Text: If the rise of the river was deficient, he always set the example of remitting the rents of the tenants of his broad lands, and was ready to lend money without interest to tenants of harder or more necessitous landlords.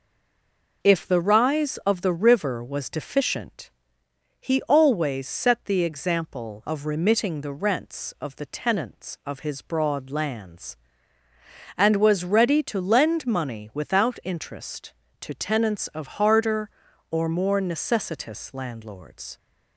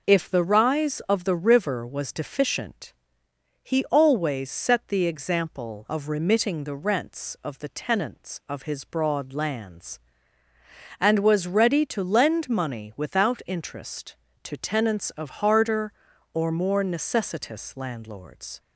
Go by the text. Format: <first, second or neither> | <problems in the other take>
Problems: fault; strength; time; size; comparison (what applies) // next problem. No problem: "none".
second | stays silent before the first word; slight; until 0.8 s; 0.8 s long